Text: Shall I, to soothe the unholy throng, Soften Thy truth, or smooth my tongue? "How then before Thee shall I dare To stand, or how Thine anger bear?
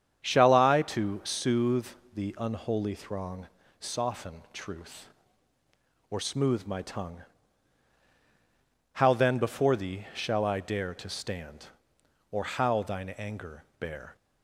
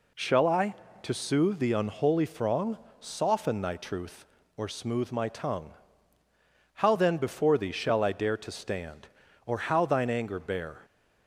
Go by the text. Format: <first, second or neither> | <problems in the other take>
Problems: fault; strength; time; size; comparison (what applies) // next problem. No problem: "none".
second | starts louder than the rest; strong; until 1.2 s; 8.5 dB // pauses between "soothe" and "the"; slight; at 1.8 s; 0.26 s long // skips "Thy"; at 4.4 s // pauses between "anger" and "bear"; slight; at 13.6 s; 0.16 s long